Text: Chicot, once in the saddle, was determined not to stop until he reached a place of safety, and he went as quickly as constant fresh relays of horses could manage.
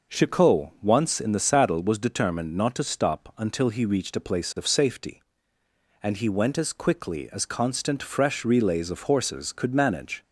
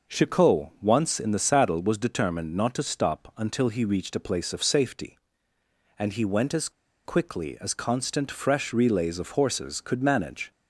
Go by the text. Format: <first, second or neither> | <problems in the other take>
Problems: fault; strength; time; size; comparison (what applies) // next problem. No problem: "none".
first | pauses between "as" and "quickly"; slight; at 6.6 s; 0.35 s long